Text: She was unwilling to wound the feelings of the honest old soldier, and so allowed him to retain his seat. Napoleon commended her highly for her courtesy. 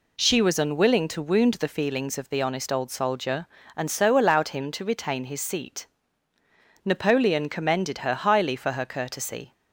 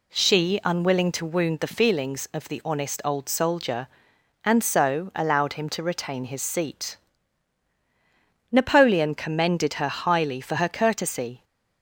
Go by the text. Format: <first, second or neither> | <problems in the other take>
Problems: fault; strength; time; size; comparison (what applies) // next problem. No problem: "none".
first | skips "was"; at 0.6 s